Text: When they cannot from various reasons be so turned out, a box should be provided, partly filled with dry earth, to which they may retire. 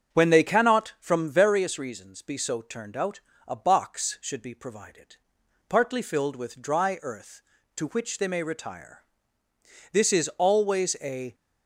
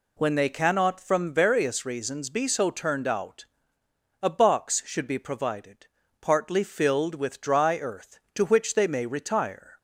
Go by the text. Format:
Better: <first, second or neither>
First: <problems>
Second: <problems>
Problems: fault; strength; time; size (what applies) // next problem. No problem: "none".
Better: second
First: starts louder than the rest; strong; until 1.1 s; 7 dB // goes on to say "This is always a"; from 9.9 s on; 1.4 s long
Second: none